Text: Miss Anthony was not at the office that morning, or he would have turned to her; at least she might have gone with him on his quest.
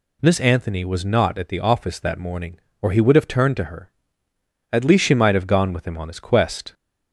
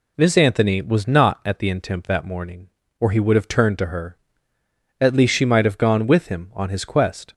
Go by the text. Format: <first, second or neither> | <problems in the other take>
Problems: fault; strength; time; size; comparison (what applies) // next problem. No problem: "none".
first | says "intemp" for "office"; at 1.6 s